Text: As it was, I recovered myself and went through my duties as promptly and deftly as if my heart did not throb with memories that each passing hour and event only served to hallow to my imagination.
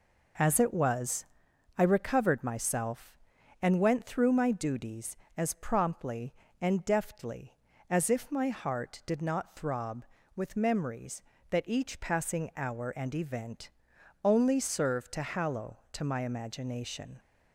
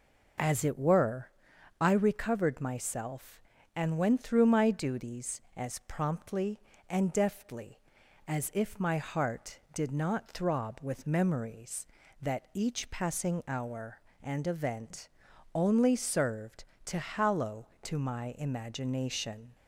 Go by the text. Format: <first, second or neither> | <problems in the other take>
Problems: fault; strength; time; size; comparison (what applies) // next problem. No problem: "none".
first | says "were" for "was"; at 0.7 s // pauses between "event" and "only"; noticeable; at 15.0 s; 0.46 s long; noticeable in the first